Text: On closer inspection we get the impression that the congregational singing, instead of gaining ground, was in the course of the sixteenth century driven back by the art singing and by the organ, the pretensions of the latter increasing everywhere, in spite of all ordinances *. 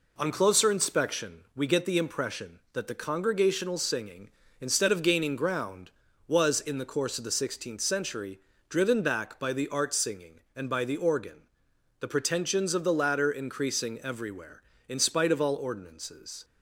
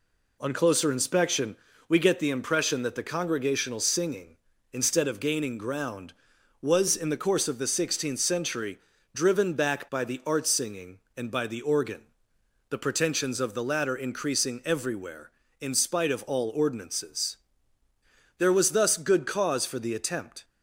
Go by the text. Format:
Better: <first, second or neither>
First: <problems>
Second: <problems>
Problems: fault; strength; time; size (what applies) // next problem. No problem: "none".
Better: first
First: pauses between "century" and "driven"; slight; at 8.3 s; 0.30 s long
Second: pauses between "inspection" and "we"; slight; at 1.5 s; 0.32 s long // pauses between "century" and "driven"; slight; at 8.7 s; 0.36 s long // goes on to say "There was thus good cause for the attempt"; strong; from 18.3 s on; 2.0 s long